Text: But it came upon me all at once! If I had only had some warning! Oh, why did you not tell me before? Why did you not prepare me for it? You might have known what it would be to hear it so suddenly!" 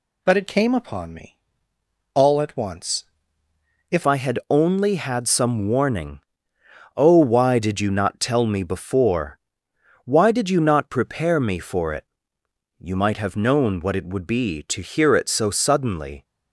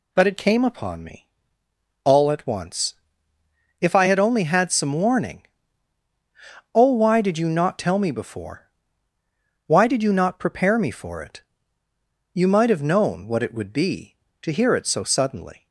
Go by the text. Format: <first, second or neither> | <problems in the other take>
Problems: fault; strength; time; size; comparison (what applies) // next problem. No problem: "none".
second | pauses between "me" and "all"; noticeable; at 1.3 s; 0.76 s long; noticeable in the second // changes voice at "I"; from 4.0 s on; 12.2 s long